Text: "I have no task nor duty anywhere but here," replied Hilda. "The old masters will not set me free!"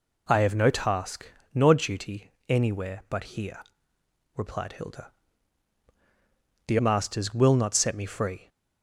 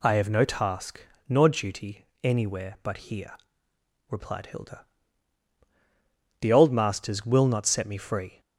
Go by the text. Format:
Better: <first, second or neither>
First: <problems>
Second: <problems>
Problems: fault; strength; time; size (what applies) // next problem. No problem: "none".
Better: second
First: pauses between "task" and "nor"; slight; at 1.3 s; 0.24 s long // pauses between "duty" and "anywhere"; slight; at 2.3 s; 0.16 s long // skips "old"; at 6.7 s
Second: pauses between "task" and "nor"; slight; at 1.0 s; 0.24 s long // pauses between "duty" and "anywhere"; slight; at 2.0 s; 0.16 s long